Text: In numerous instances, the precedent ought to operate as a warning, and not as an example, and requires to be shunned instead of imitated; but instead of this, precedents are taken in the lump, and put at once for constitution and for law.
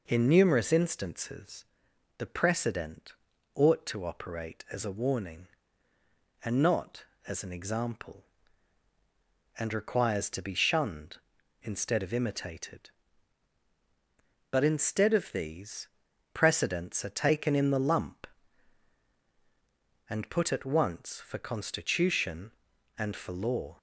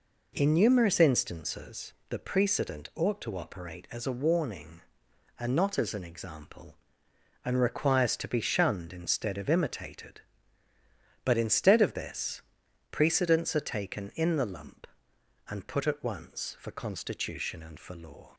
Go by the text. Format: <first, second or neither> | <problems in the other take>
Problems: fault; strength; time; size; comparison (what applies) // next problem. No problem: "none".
second | pauses between "precedent" and "ought"; at 3.1 s; 0.42 s long // says "these" for "this"; at 15.3 s